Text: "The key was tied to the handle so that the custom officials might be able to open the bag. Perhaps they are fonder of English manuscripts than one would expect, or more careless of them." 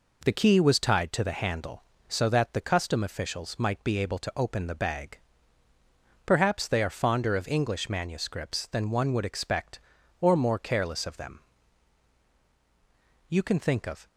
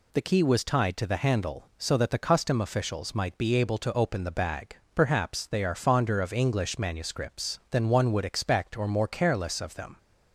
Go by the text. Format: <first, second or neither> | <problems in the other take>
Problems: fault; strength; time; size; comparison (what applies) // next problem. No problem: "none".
second | goes on to say "You can think of"; noticeable; from 13.2 s on; 0.78 s long